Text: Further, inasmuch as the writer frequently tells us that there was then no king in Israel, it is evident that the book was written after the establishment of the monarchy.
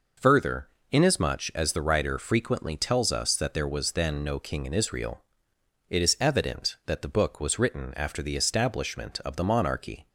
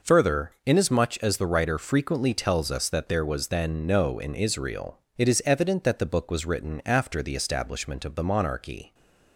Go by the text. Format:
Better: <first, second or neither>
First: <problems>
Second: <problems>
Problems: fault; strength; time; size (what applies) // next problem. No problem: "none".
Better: first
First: none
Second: skips "king"; at 4.1 s